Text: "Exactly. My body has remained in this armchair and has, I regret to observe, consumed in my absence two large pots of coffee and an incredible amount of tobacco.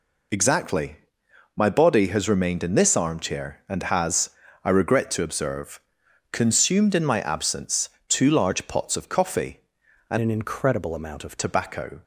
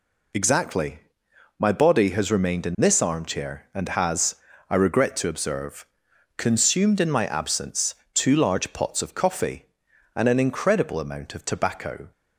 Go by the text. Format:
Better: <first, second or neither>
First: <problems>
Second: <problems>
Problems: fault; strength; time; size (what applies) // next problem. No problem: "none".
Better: second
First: pauses between "absence" and "two"; slight; at 7.8 s; 0.20 s long // changes voice from "an" to "of"; from 10.1 to 11.3 s; 1.2 s long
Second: pauses between "absence" and "two"; slight; at 7.9 s; 0.20 s long